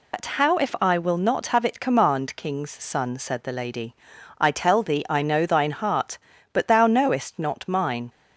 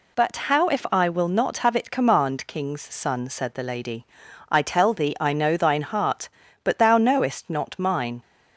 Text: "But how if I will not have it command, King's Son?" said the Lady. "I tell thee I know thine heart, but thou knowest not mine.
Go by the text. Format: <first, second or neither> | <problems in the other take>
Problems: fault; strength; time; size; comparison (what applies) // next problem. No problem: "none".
second | loses the start of "But"; at 0.1 s; 75 ms